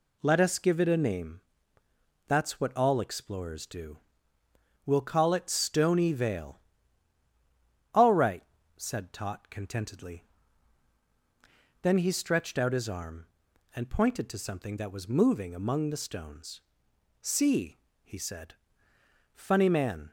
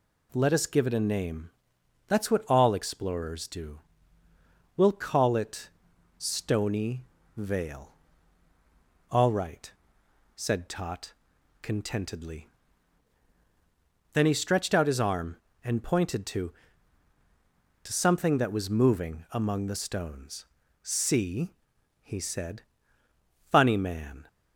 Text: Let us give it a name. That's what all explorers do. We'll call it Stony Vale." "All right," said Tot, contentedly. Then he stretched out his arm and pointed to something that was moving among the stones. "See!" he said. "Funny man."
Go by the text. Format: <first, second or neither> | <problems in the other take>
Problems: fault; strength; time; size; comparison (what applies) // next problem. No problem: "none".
first | pauses between "it" and "Stony"; noticeable; at 5.6 s; 0.50 s long // pauses between "Stony" and "Vale"; slight; at 7.0 s; 0.28 s long // says "to" twice; at 17.8 s